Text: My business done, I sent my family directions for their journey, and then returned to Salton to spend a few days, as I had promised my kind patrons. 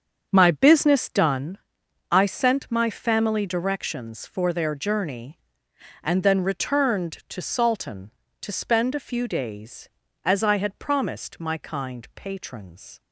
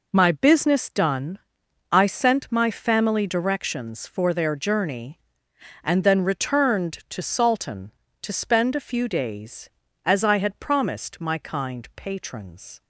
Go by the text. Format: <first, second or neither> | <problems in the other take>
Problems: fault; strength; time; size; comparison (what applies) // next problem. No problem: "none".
second | starts louder than the rest; strong; until 1.6 s; 7.5 dB